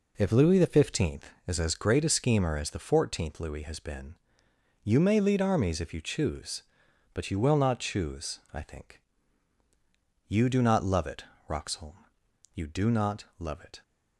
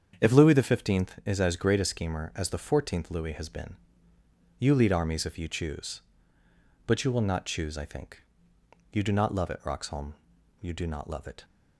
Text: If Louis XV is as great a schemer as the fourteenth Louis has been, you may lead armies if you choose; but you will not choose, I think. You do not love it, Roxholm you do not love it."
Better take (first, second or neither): first